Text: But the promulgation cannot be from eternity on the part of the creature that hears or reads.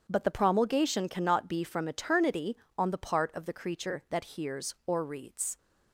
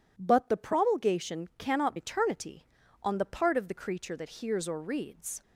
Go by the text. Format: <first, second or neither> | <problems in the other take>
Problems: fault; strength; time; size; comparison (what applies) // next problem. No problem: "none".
first | skips "be from"; at 1.9 s